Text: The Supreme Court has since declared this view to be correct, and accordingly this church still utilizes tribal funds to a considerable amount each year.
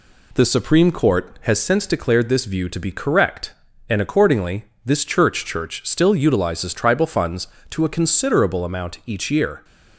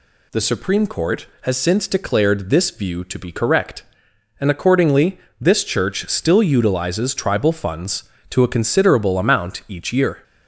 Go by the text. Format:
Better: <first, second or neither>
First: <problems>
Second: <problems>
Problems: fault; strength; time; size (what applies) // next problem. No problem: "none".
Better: second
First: pauses between "accordingly" and "this"; slight; at 4.6 s; 0.18 s long // says "church" twice; at 5.4 s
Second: pauses between "accordingly" and "this"; slight; at 5.1 s; 0.24 s long